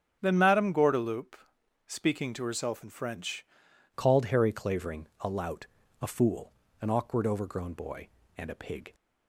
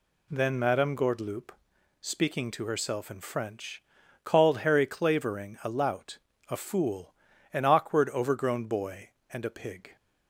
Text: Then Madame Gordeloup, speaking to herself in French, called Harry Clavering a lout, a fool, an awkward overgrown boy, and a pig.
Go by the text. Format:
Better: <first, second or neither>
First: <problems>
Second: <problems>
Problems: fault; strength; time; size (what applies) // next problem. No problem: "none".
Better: second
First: starts louder than the rest; strong; until 1.2 s; 9 dB // changes voice at "called"; from 3.9 s on; 5.0 s long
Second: none